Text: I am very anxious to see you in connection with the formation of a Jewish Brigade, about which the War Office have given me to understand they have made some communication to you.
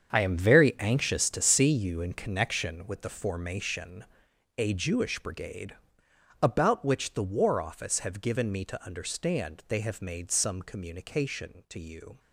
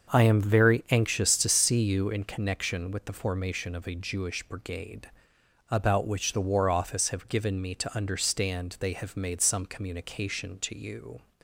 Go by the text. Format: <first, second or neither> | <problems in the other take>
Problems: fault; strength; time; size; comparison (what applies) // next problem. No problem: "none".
second | starts louder than the rest; strong; until 1.1 s; 7.5 dB; also in the second // skips "of"; at 4.3 s